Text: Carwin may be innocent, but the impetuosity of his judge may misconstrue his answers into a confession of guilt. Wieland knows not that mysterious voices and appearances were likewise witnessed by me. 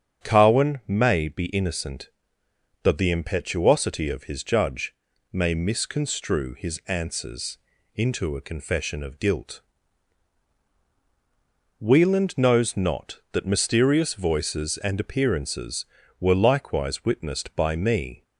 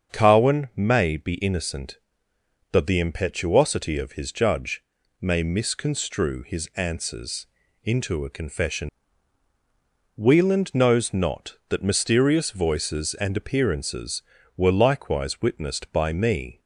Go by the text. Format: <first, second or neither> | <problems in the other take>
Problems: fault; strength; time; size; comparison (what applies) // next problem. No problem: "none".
first | starts louder than the rest; until 1.1 s; 7 dB; strong in the first // pauses between "judge" and "may"; at 4.8 s; 0.40 s long; also in the first // pauses between "answers" and "into"; at 7.4 s; 0.38 s long; also in the first // skips "of guilt"; at 9.5 s